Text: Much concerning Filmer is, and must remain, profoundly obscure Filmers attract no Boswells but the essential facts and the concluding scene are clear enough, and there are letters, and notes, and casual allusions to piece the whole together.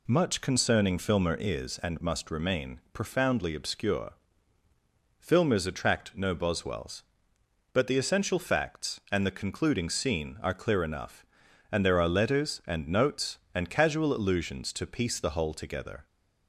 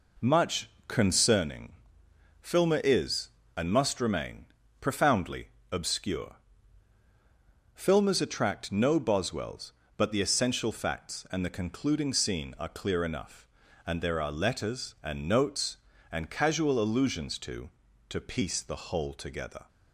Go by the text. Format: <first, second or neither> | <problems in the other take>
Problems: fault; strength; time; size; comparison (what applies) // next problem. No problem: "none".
first | pauses between "Much" and "concerning"; slight; at 0.6 s; 0.20 s long // pauses between "concerning" and "Filmer"; noticeable; at 1.7 s; 0.68 s long // pauses between "profoundly" and "obscure"; slight; at 5.4 s; 0.20 s long // pauses between "obscure" and "Filmers"; strong; at 6.3 s; 1.4 s long; also in the first // says "to" twice; at 18.0 s